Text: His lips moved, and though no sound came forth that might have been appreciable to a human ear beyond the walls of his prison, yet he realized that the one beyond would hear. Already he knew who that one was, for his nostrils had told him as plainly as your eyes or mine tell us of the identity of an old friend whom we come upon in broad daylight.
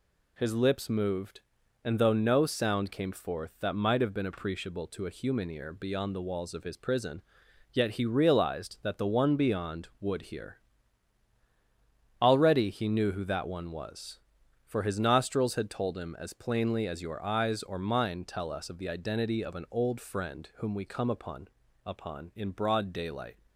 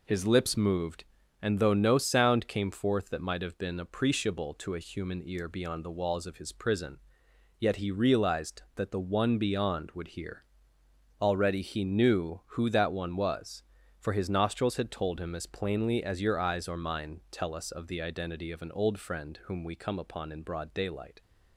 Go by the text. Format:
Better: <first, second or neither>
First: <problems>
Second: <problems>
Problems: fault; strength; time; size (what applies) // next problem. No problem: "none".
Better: second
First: says "upon" twice; at 21.8 s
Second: none